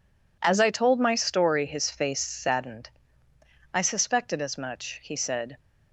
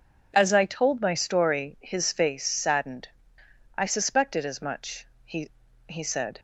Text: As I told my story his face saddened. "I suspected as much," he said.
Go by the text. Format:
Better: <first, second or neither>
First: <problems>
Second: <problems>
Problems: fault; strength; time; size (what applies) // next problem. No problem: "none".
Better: first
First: none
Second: says "he" twice; at 5.8 s